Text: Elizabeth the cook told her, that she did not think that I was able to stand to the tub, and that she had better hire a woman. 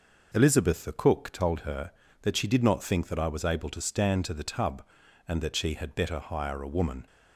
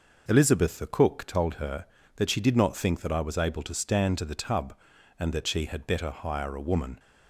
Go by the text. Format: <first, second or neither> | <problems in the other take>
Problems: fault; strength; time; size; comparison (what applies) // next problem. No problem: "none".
neither | none